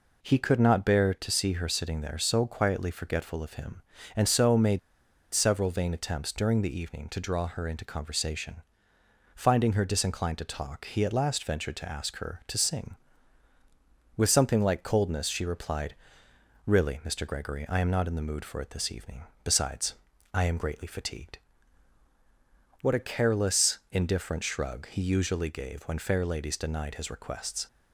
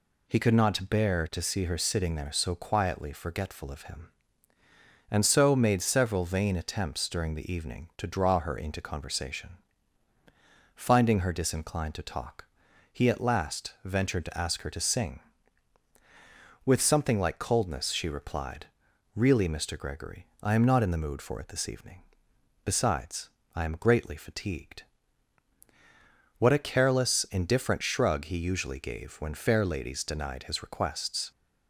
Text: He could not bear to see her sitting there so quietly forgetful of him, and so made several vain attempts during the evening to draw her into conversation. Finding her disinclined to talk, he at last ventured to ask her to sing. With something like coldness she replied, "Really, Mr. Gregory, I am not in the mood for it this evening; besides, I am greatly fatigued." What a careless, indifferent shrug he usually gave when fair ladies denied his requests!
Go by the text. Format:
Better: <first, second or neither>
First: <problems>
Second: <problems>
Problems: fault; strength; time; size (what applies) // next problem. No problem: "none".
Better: second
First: pauses between "made" and "several"; noticeable; at 4.7 s; 0.55 s long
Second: none